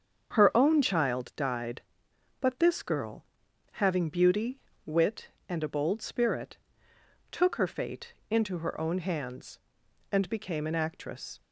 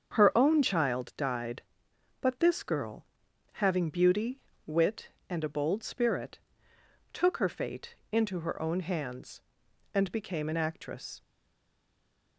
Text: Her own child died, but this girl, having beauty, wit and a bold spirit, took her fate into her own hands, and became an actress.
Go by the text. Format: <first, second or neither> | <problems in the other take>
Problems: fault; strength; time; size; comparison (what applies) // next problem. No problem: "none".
first | starts louder than the rest; strong; until 1.1 s; 7 dB; strong in the first // pauses between "fate" and "into"; slight; at 7.9 s; 0.18 s long; slight in the first // stays silent after the last word; noticeable; from 11.2 s on; 1.1 s long